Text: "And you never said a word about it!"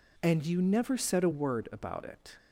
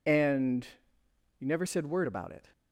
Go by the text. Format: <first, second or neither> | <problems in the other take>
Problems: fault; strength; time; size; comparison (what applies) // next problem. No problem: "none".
first | pauses between "And" and "you"; noticeable; at 0.6 s; 0.72 s long // skips "a"; at 1.8 s